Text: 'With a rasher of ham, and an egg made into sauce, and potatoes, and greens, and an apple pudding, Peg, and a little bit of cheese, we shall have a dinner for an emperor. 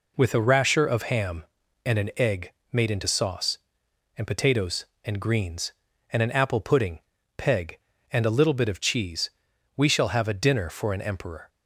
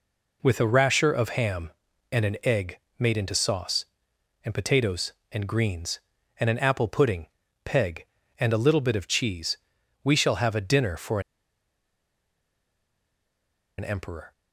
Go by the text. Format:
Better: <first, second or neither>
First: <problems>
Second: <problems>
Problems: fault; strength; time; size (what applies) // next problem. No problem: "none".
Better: first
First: pauses between "egg" and "made"; slight; at 2.5 s; 0.20 s long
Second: pauses between "egg" and "made"; slight; at 2.7 s; 0.20 s long // pauses between "for" and "an"; strong; at 11.1 s; 2.5 s long